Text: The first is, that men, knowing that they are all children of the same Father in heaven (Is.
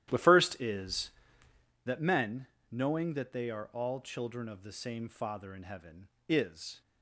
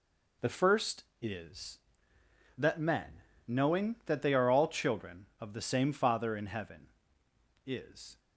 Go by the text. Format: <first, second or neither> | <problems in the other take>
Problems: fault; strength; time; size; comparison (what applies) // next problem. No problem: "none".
second | starts louder than the rest; strong; until 1.7 s; 12 dB